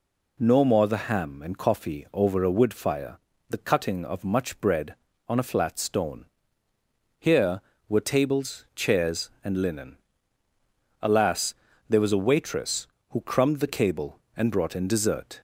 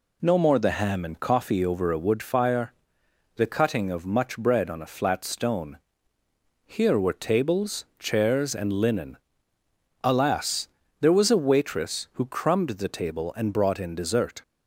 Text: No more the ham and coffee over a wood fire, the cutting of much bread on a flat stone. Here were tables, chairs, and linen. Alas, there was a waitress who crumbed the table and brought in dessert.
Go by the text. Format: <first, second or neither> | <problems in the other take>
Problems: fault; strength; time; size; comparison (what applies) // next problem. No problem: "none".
second | says "cable" for "table"; at 13.6 s